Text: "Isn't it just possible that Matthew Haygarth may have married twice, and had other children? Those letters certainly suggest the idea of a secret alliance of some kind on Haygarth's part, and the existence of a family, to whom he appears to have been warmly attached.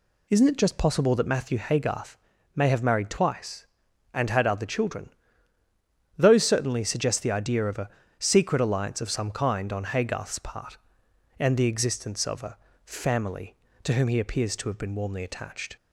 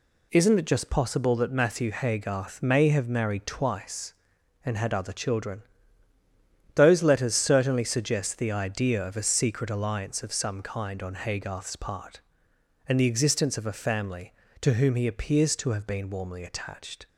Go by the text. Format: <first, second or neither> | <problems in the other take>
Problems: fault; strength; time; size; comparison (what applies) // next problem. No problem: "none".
second | pauses between "Haygarth" and "may"; at 2.1 s; 0.40 s long // skips "letters"; at 6.4 s // pauses between "a" and "secret"; slight; at 7.8 s; 0.28 s long // pauses between "a" and "family"; slight; at 12.5 s; 0.30 s long